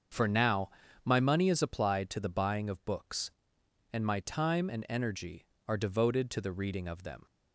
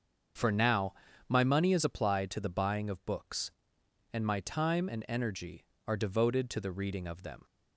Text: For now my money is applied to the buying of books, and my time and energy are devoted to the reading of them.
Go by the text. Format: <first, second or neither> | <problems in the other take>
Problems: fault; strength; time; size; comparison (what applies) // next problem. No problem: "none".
neither | starts louder than the rest; the same in both // pauses between "now" and "my"; slight; the same in both